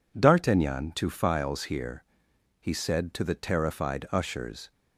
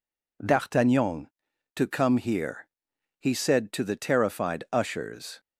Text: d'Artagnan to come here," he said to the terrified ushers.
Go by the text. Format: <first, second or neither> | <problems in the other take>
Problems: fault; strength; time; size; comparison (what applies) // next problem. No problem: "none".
second | says "files" for "come"; at 1.0 s